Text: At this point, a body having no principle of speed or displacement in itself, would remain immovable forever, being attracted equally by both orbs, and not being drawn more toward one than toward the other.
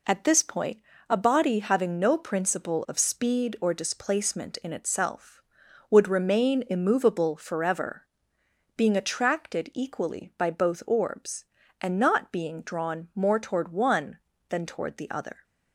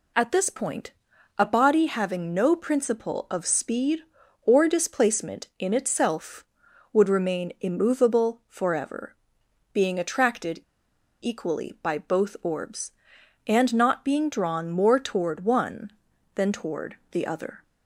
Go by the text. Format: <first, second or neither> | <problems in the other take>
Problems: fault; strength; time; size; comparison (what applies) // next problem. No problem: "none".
first | pauses between "attracted" and "equally"; noticeable; at 10.5 s; 0.62 s long // pauses between "toward" and "the"; slight; at 16.9 s; 0.16 s long